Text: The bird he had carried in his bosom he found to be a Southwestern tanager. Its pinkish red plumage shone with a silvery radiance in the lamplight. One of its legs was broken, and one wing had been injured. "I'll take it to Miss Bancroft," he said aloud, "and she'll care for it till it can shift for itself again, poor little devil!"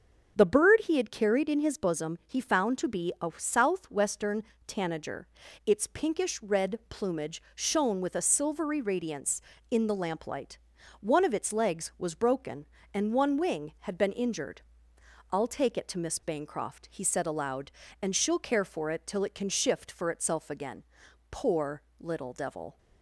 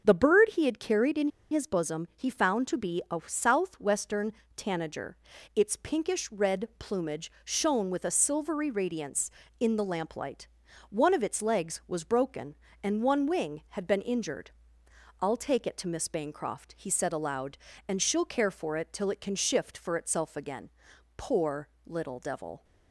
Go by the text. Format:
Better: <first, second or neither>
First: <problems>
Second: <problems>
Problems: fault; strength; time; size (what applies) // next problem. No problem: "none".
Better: first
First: starts louder than the rest; strong; until 1.3 s; 7.5 dB // pauses between "Southwestern" and "tanager"; slight; at 4.4 s; 0.24 s long // pauses between "poor" and "little"; slight; at 21.8 s; 0.18 s long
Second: starts louder than the rest; strong; until 1.0 s; 7.5 dB // pauses between "in" and "his"; slight; at 1.2 s; 0.22 s long // pauses between "Southwestern" and "tanager"; slight; at 4.3 s; 0.24 s long // pauses between "poor" and "little"; slight; at 21.6 s; 0.18 s long